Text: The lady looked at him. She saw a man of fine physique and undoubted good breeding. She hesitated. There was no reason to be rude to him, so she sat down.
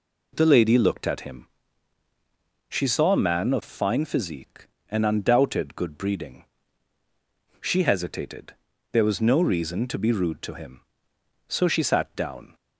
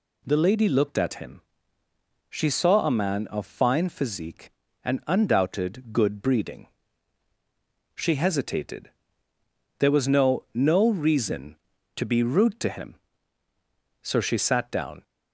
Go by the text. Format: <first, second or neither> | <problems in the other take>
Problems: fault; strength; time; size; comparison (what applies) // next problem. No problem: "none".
first | says "no" twice; at 10.5 s